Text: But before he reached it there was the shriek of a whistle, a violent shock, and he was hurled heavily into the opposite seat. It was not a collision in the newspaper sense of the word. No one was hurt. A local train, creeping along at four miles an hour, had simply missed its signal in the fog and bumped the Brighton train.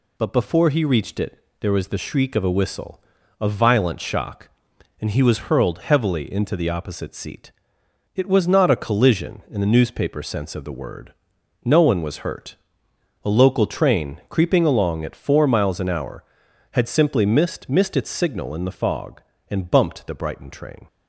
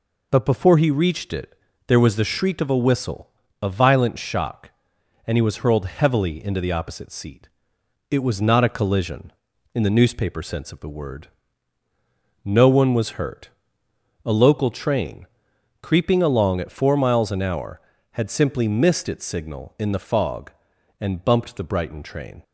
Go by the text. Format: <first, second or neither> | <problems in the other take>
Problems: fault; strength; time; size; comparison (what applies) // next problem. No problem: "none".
second | pauses between "it" and "there"; slight; at 1.3 s; 0.22 s long; slight in the second // says "missed" twice; at 17.6 s